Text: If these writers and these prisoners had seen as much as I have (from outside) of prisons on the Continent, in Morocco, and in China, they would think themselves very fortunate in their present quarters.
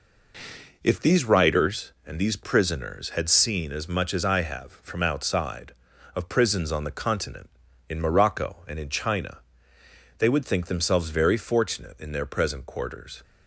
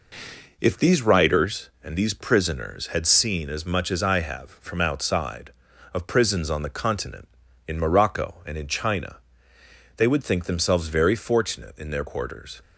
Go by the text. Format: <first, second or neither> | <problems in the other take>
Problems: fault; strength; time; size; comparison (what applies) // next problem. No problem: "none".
first | skips "present"; at 12.0 s